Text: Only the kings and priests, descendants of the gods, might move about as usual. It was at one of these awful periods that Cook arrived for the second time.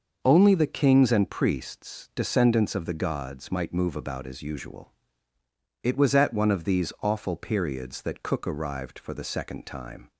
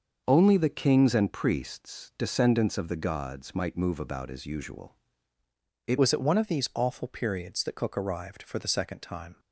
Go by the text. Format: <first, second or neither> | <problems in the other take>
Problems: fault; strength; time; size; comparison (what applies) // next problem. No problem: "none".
first | starts louder than the rest; until 1.2 s; 6 dB; also in the first // changes voice at "was"; from 5.9 s on; 3.4 s long